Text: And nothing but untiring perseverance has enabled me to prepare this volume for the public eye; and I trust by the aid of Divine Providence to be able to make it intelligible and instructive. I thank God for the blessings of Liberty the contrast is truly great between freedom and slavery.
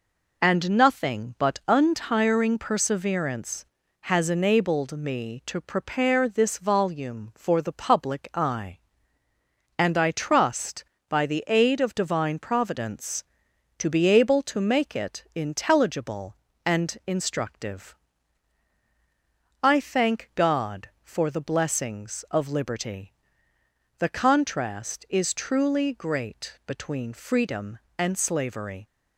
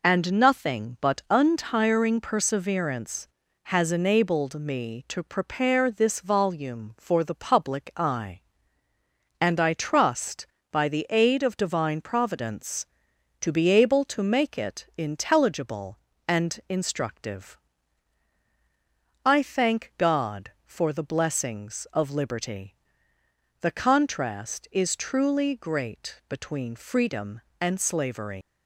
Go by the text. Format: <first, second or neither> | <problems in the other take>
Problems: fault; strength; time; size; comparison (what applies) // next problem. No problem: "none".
first | pauses between "Liberty" and "the"; noticeable; at 22.7 s; 0.88 s long; noticeable in the first // leaves "slavery" unfinished; at 28.4 s; 60 ms